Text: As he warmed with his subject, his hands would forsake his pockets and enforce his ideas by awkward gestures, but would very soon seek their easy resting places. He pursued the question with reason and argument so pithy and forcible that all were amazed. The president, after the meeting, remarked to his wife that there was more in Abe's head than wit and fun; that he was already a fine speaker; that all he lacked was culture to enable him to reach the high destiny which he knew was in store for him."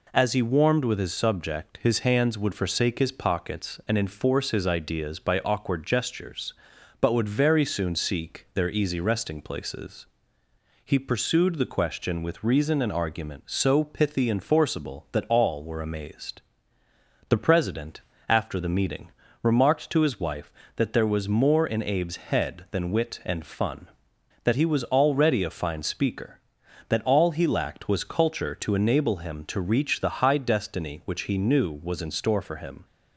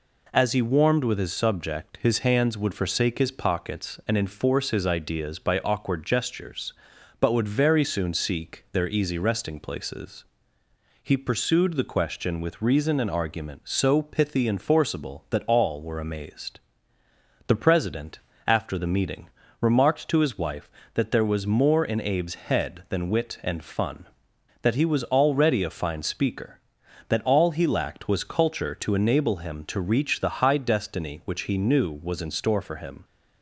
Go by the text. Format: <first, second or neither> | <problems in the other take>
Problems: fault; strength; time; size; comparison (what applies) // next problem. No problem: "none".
neither | none